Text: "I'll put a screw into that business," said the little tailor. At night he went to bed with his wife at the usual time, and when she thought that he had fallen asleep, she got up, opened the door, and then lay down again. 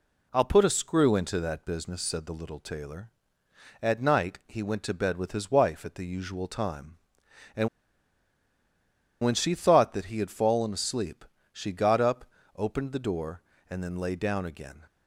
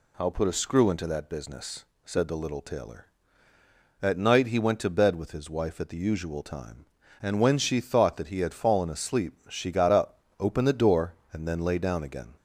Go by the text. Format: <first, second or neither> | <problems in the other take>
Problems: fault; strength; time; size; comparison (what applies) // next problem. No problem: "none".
second | pauses between "and" and "when"; strong; at 7.6 s; 1.5 s long